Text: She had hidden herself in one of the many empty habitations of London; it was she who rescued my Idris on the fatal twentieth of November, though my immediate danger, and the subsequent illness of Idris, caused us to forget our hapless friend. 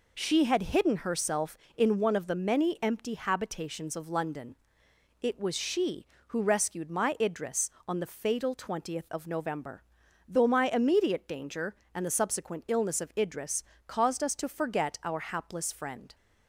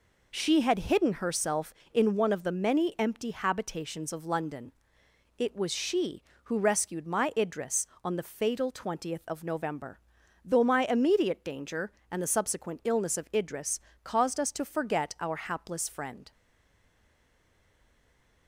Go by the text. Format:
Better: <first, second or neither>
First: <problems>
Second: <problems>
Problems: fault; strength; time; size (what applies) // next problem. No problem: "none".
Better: first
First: none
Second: stays silent after the last word; from 16.3 s on; 2.1 s long